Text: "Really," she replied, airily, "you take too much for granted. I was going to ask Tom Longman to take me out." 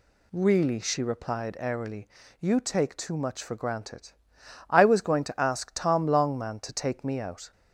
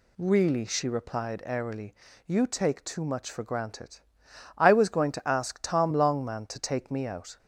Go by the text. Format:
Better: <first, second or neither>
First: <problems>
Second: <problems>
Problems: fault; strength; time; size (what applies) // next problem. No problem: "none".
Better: neither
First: none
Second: none